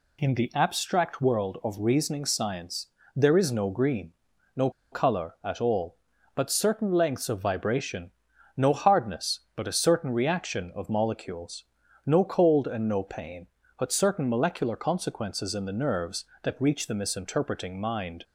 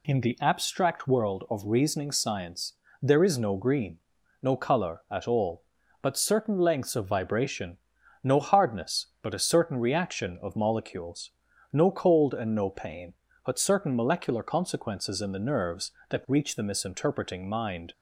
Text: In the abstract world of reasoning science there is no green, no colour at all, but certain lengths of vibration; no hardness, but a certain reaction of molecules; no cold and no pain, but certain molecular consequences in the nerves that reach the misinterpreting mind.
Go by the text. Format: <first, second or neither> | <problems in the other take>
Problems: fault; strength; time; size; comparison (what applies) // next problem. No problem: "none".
second | pauses between "science" and "there"; slight; at 2.8 s; 0.28 s long; slight in the second // pauses between "no" and "colour"; slight; at 4.6 s; 0.22 s long